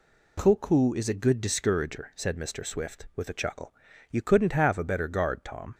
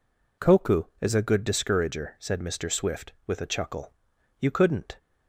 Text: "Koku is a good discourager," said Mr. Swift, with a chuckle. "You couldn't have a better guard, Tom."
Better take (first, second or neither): first